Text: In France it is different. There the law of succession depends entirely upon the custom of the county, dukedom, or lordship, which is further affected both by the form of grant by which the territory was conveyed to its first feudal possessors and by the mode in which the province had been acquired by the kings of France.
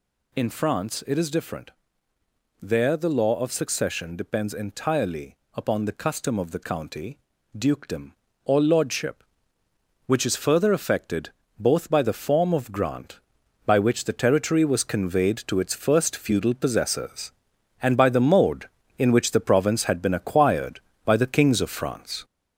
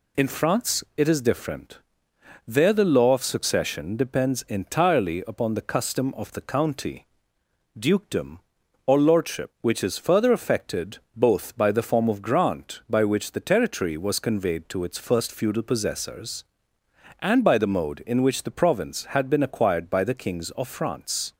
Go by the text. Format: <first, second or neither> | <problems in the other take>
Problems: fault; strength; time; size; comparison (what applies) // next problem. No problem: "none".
second | gets louder; noticeable; throughout; 5 dB // pauses between "entirely" and "upon"; slight; at 5.3 s; 0.18 s long // pauses between "affected" and "both"; slight; at 11.2 s; 0.30 s long; slight in the second